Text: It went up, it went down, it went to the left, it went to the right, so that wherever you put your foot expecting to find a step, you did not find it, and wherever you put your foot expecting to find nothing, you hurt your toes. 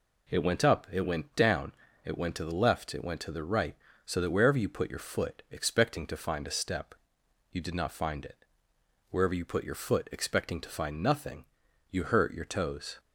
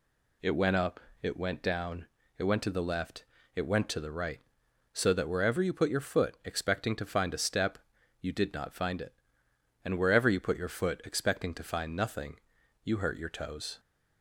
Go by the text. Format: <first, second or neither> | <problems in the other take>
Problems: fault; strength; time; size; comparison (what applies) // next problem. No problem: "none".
second | skips "and"; at 8.7 s